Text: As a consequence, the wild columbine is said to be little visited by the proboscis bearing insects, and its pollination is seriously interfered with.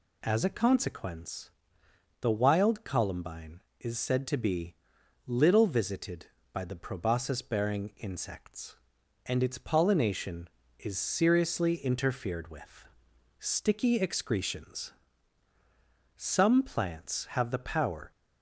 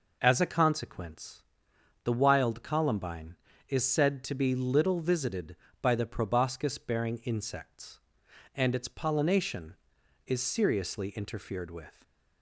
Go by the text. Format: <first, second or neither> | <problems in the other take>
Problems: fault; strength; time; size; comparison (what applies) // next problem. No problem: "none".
second | pauses between "be" and "little"; noticeable; at 4.7 s; 0.54 s long // goes on to say "Sticky excretions Some plants have the power"; strong; from 13.3 s on; 4.7 s long